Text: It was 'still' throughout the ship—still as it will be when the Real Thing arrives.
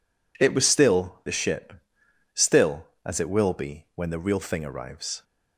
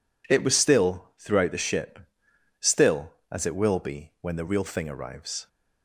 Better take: second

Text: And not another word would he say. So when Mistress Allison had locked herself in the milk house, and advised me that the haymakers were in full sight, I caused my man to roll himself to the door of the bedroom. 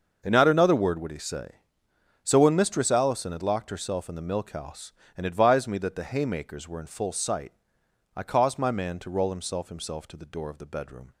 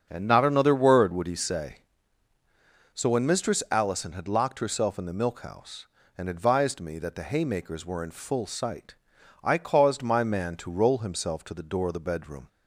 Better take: second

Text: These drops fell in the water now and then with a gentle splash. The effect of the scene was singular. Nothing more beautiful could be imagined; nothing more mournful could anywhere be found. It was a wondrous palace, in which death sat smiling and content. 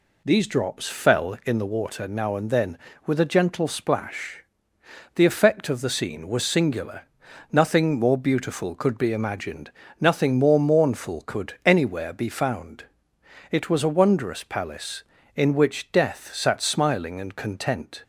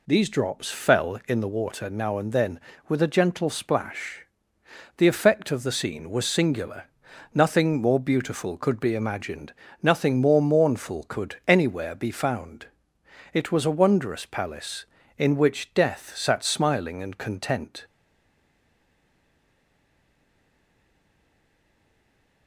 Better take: first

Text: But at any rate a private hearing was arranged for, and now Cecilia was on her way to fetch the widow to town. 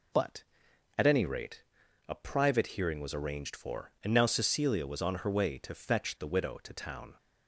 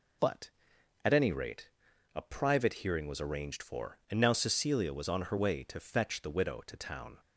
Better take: neither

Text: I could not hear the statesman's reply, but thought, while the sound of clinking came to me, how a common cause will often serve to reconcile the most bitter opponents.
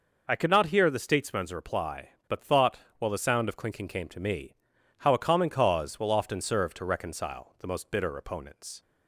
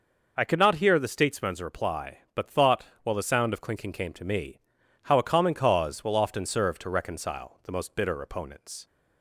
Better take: neither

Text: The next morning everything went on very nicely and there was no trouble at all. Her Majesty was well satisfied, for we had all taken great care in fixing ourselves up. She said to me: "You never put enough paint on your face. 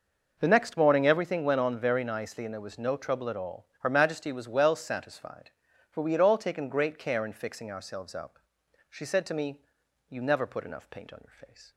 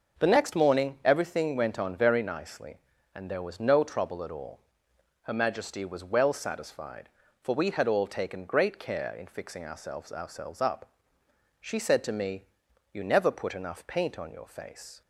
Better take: first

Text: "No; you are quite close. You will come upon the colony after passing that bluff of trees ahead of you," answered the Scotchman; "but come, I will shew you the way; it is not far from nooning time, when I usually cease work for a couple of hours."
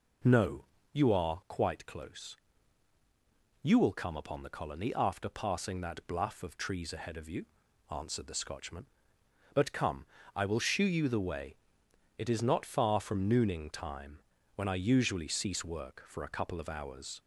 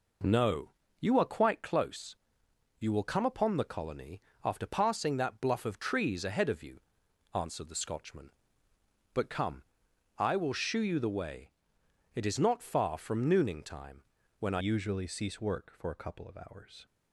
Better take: first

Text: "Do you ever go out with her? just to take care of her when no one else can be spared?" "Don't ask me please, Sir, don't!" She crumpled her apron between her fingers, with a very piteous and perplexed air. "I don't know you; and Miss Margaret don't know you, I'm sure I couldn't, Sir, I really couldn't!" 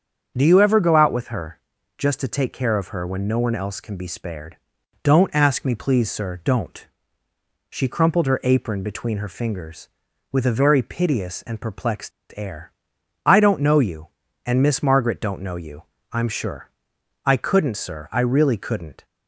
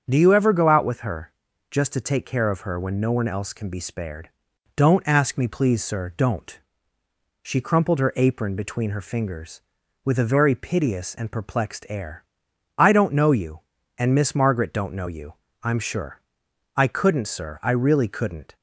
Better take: second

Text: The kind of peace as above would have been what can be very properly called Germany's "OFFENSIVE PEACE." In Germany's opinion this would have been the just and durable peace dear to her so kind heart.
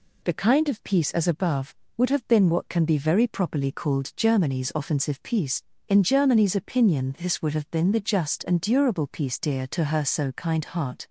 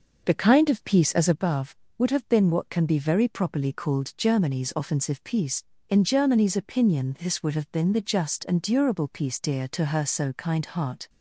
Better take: first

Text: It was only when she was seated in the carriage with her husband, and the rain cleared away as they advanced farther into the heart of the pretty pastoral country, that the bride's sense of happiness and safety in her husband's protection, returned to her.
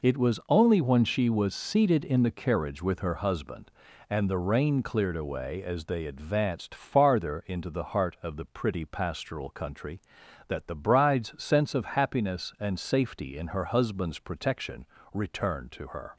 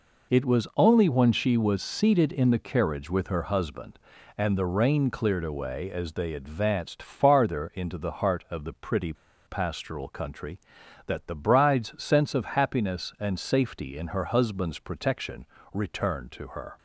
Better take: first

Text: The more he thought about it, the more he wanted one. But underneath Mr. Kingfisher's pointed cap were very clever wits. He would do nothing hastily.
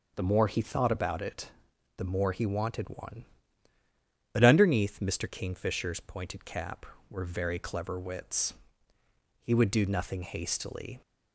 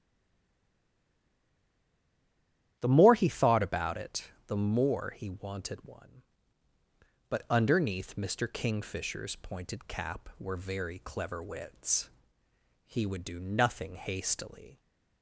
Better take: first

